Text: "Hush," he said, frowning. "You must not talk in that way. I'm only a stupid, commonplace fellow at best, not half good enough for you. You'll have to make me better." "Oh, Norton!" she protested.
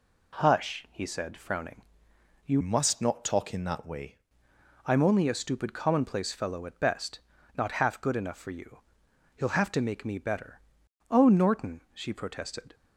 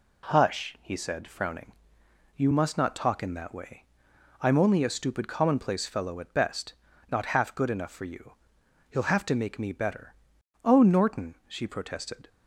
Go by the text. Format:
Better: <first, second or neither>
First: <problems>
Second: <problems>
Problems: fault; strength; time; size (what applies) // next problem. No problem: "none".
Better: second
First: changes voice from "must" to "way"; from 2.6 to 4.1 s; 1.5 s long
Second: none